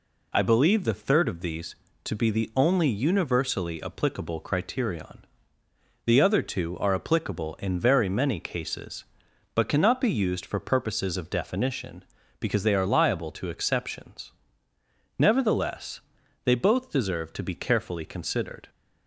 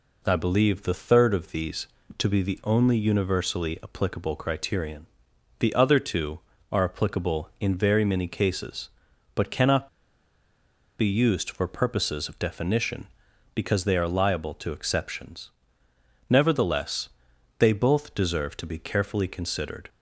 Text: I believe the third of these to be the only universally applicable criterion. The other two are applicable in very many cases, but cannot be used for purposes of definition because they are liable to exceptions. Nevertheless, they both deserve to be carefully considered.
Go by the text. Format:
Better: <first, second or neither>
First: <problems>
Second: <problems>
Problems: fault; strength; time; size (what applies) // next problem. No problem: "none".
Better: first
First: none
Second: pauses between "cannot" and "be"; at 9.8 s; 1.1 s long